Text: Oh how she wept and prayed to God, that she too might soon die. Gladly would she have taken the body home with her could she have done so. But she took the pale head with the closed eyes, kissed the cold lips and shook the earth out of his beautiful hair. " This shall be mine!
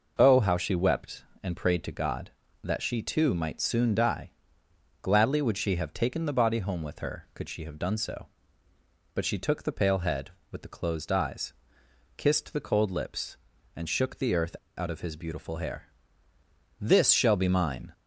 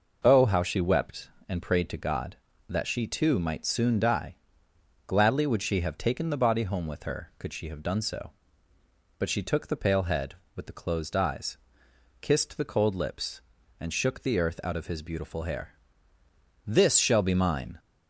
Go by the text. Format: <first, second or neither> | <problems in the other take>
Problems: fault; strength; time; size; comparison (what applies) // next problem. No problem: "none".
second | pauses between "earth" and "out"; slight; at 14.5 s; 0.20 s long